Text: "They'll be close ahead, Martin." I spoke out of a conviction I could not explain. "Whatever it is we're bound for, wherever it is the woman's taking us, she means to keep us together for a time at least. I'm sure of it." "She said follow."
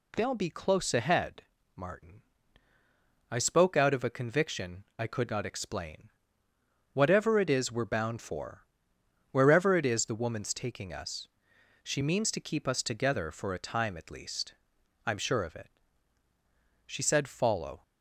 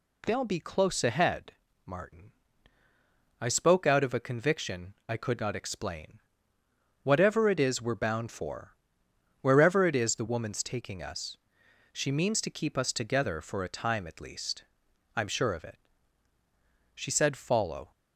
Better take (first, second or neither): neither